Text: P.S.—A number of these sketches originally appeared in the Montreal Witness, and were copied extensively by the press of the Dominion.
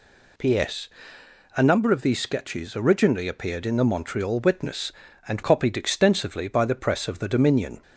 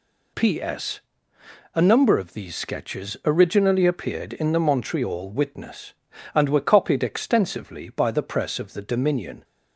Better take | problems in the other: second | skips "were"; at 5.4 s

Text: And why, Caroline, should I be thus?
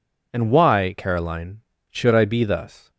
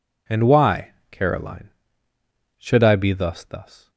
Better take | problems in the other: first | says "thus" twice; at 3.4 s

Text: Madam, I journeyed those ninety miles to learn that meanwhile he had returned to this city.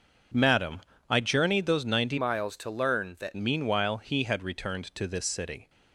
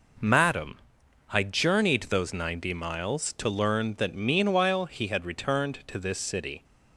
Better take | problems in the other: second | changes voice from "miles" to "that"; from 2.1 to 3.3 s; 1.2 s long

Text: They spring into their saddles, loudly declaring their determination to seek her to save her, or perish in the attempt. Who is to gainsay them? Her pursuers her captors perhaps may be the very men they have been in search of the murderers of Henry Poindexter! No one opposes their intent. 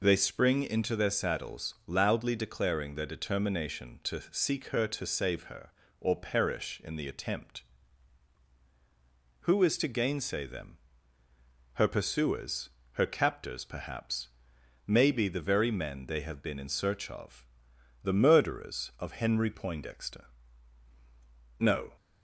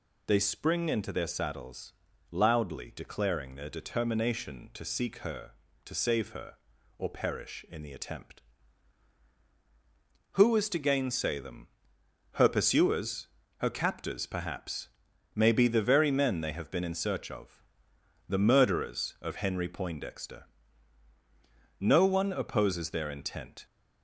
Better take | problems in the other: second | pauses between "pursuers" and "her"; slight; at 12.6 s; 0.24 s long; slight in the second // pauses between "perhaps" and "may"; noticeable; at 14.2 s; 0.60 s long; also in the second // pauses between "of" and "the"; noticeable; at 17.4 s; 0.58 s long; noticeable in the second // stops before "one opposes their intent"; at 21.9 s

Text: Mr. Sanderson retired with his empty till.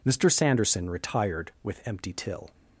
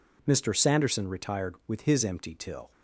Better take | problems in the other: second | skips "his"; at 1.8 s

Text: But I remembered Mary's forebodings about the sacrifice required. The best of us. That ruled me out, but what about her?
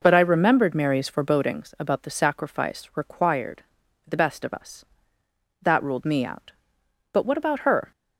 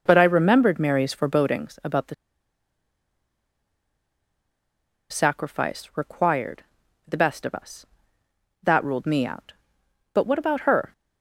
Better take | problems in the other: first | pauses between "the" and "sacrifice"; strong; at 2.1 s; 2.9 s long

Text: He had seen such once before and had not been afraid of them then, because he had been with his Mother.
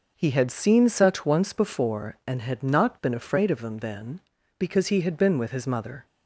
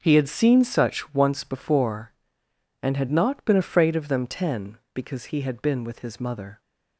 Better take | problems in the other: first | starts louder than the rest; until 1.0 s; 6 dB // says "ten" for "then"; at 4.2 s

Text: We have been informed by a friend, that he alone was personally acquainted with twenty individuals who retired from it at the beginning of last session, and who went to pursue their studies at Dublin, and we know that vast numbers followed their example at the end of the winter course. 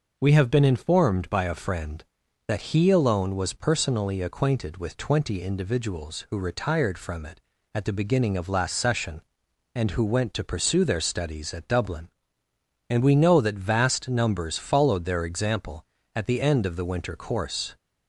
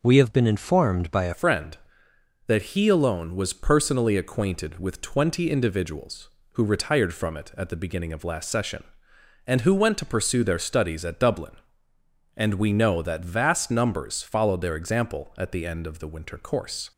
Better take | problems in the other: first | changes voice at "friend"; from 1.3 s on; 15.6 s long

